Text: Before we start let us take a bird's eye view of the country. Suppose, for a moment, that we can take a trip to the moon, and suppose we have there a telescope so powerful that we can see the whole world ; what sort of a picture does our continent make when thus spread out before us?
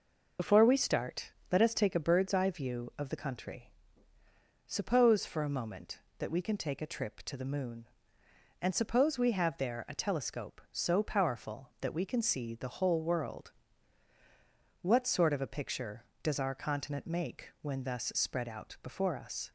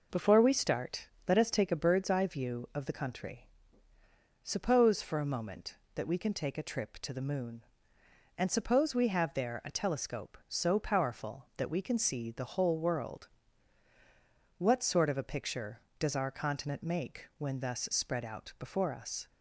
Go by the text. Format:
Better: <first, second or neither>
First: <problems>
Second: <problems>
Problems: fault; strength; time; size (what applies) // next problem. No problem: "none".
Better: second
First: loses the start of "Before"; at 0.3 s; 40 ms // pauses between "start" and "let"; slight; at 1.3 s; 0.20 s long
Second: pauses between "start" and "let"; slight; at 1.0 s; 0.20 s long